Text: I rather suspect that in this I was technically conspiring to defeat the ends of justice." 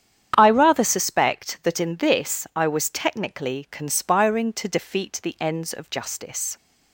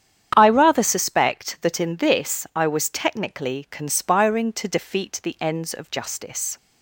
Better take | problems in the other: neither | starts louder than the rest; strong; the same in both

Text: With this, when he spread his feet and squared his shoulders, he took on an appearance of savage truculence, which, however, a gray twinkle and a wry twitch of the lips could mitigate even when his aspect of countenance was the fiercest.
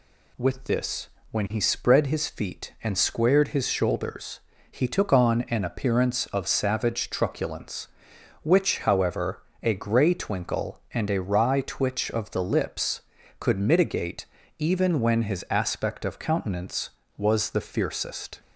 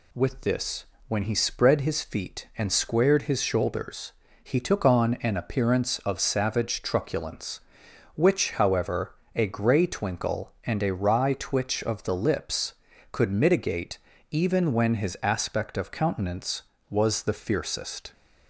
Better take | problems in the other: neither | pauses between "mitigate" and "even"; slight; the same in both

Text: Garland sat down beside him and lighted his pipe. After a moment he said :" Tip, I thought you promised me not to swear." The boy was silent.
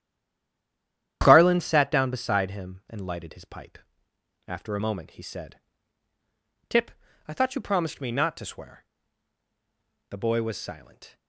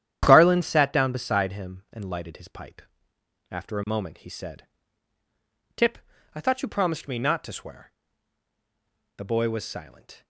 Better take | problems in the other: second | stays silent before the first word; noticeable; until 1.2 s; 1.2 s long // starts louder than the rest; strong; until 2.2 s; 11 dB; strong in the second

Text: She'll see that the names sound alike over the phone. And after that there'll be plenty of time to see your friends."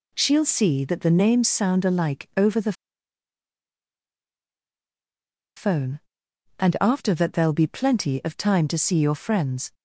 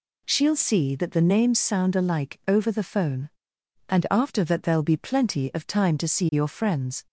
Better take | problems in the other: second | pauses between "the" and "phone"; strong; at 2.7 s; 2.8 s long

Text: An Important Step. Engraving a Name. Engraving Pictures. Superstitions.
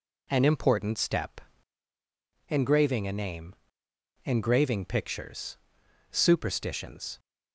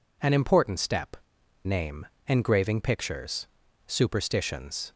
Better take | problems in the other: first | skips "Engraving a"; at 1.4 s

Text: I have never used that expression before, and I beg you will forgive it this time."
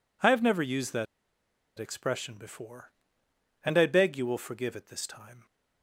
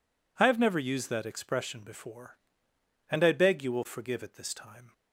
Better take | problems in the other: second | pauses between "that" and "expression"; noticeable; at 1.0 s; 0.73 s long

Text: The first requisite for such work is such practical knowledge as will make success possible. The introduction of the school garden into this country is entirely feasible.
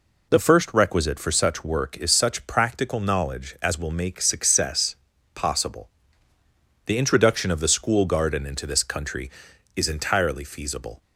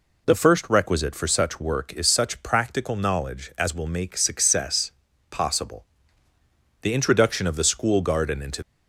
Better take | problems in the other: first | pauses between "success" and "possible"; at 4.9 s; 0.38 s long; also in the first // stops before "this country is entirely feasible"; at 8.6 s

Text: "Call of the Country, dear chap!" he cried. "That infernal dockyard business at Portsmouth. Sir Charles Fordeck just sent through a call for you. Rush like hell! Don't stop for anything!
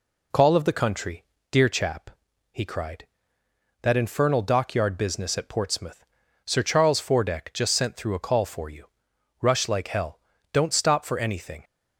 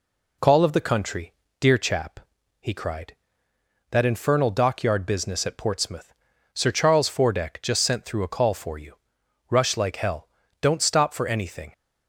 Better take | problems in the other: neither | none

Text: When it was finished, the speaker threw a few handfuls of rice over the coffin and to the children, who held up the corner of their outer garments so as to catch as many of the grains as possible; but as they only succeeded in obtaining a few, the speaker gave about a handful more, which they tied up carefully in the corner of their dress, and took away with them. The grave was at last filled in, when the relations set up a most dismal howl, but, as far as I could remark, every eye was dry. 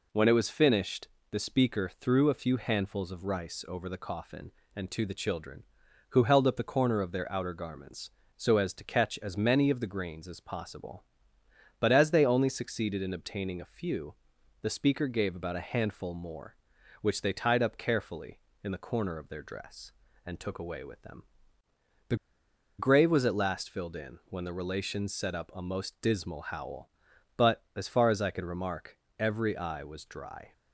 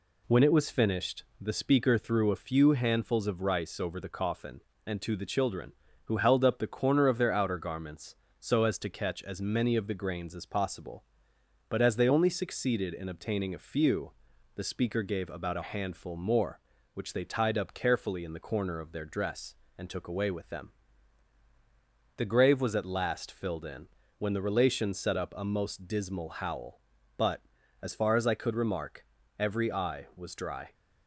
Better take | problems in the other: second | pauses between "The" and "grave"; noticeable; at 22.1 s; 0.63 s long

